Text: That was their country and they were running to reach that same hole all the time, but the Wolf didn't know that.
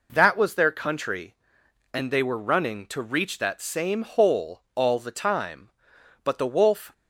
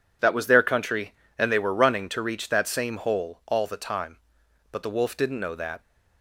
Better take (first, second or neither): second